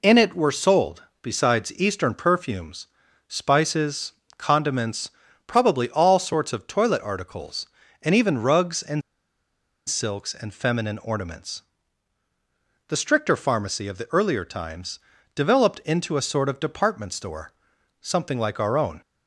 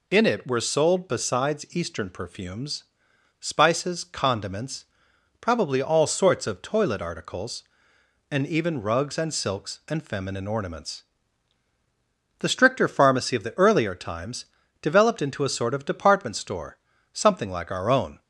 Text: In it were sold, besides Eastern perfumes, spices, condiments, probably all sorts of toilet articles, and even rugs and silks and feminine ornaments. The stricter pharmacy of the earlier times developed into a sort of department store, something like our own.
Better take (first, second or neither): second